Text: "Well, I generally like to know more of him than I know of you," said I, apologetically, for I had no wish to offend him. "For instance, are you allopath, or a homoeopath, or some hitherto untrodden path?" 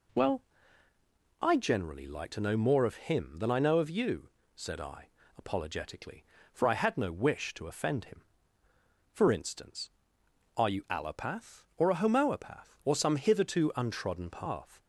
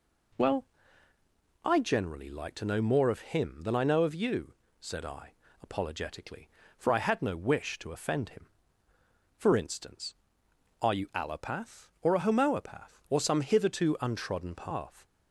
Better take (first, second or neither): neither